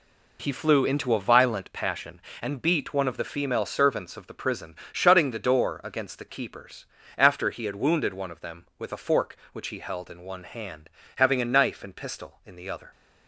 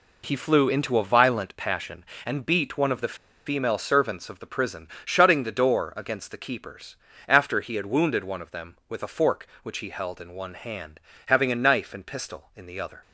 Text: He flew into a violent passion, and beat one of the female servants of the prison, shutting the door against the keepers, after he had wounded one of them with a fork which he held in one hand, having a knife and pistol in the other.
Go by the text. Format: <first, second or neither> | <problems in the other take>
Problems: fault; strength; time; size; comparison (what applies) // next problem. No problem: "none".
first | pauses between "the" and "female"; slight; at 3.1 s; 0.31 s long